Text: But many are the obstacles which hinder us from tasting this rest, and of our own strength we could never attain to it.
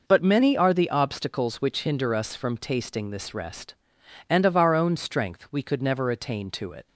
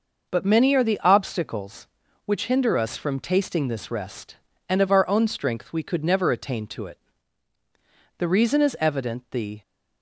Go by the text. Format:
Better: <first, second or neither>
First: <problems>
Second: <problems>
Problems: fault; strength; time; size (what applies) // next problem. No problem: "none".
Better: first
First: none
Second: goes on to say "The reason is evident the"; from 8.1 s on; 1.4 s long